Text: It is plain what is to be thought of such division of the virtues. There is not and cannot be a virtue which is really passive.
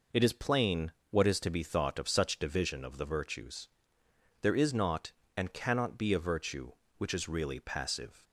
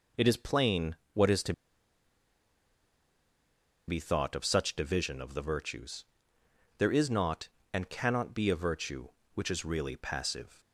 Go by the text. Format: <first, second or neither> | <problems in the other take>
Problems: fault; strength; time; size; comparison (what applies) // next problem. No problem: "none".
first | pauses between "plain" and "what"; slight; at 0.9 s; 0.18 s long; slight in the first // pauses between "to" and "be"; strong; at 1.5 s; 2.3 s long